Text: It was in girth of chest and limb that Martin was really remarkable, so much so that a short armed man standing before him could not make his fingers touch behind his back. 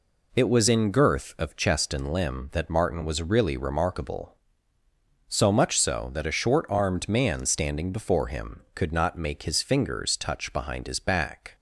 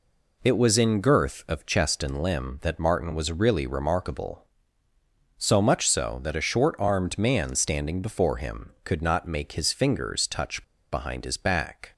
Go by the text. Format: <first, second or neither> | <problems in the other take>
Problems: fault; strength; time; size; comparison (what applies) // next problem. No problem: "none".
first | pauses between "touch" and "behind"; slight; at 10.6 s; 0.28 s long